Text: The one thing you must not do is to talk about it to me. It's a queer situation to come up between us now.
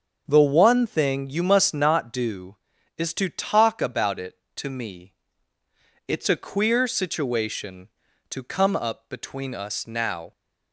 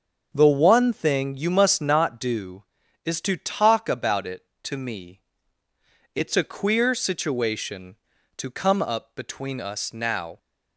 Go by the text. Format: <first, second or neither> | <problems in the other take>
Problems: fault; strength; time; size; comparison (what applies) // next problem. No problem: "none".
neither | starts louder than the rest; the same in both